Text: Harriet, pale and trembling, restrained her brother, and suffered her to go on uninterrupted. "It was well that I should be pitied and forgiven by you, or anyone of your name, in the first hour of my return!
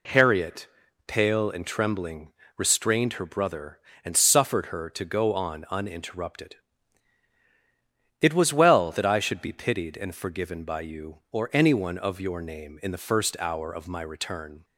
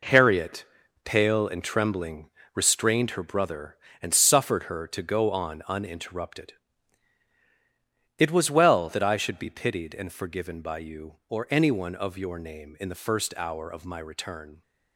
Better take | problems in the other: first | gets quieter; strong; throughout; 9.5 dB

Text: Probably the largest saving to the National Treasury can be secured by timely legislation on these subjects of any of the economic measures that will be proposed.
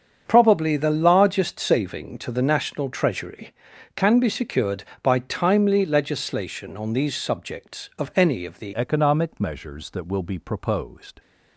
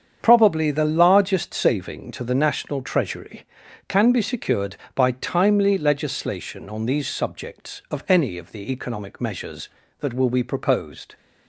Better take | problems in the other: second | starts louder than the rest; strong; until 1.2 s; 7.5 dB; strong in the second // changes voice at "economic"; from 8.7 s on; 2.4 s long

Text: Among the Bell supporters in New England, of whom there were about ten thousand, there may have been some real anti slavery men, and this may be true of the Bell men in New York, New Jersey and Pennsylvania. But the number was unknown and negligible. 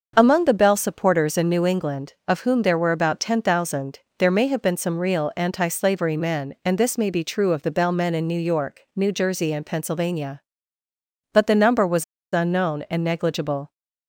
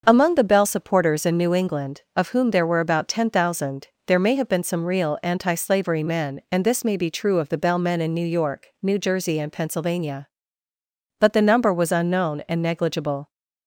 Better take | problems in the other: second | starts louder than the rest; until 1.1 s; 6.5 dB; also in the second // pauses between "was" and "unknown"; slight; at 12.0 s; 0.28 s long

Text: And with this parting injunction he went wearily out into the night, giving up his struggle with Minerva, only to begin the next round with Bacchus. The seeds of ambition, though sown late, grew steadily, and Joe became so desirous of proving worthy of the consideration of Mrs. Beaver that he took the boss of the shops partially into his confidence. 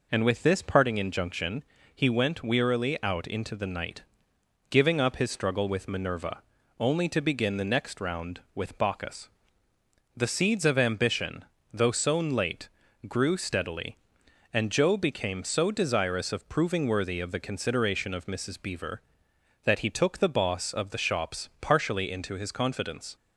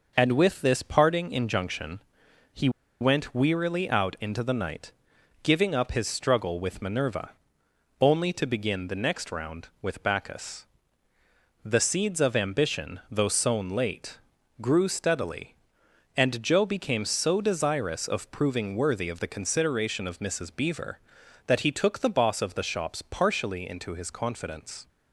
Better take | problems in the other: first | pauses between "injunction" and "he"; noticeable; at 2.0 s; 0.54 s long; slight in the first // pauses between "he" and "went"; slight; at 2.6 s; 0.31 s long

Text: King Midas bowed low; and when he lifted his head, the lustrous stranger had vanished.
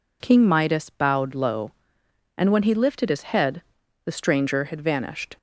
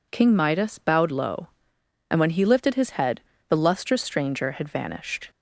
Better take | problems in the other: second | skips "lustrous"; at 4.1 s

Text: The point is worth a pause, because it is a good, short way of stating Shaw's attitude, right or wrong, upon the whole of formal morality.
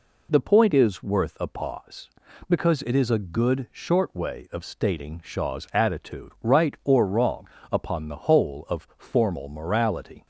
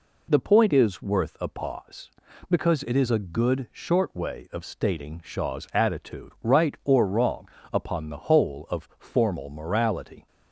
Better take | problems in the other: neither | none

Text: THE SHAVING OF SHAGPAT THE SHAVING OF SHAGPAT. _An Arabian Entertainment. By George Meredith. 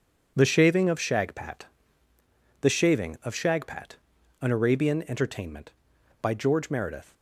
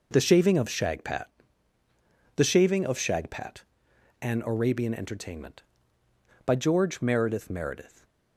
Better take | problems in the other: first | pauses between "SHAGPAT" and "THE"; at 1.2 s; 1.0 s long; noticeable in the first // says "Meredith" twice; at 7.4 s // stays silent after the last word; slight; from 7.8 s on; 0.5 s long

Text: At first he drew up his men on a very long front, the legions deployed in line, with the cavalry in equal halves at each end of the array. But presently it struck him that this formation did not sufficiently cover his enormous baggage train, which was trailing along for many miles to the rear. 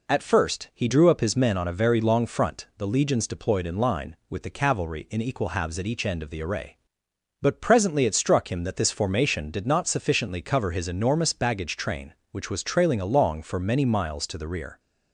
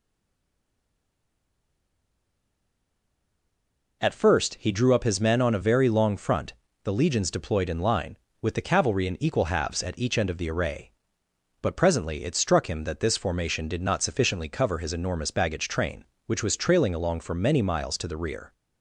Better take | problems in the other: first | stays silent before the first word; strong; until 4.0 s; 4.0 s long

